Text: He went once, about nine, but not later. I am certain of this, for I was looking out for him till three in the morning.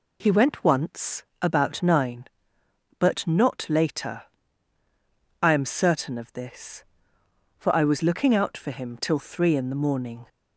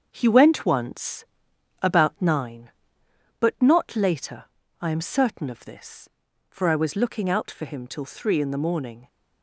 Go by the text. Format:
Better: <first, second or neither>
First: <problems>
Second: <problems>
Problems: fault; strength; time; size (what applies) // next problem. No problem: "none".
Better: first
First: none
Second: gets quieter; throughout; 6.5 dB